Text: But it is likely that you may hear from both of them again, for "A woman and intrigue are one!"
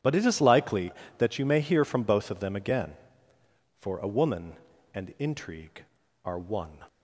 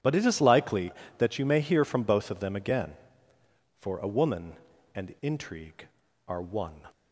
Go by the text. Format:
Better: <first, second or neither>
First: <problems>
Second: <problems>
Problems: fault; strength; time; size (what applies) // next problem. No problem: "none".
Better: neither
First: none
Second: none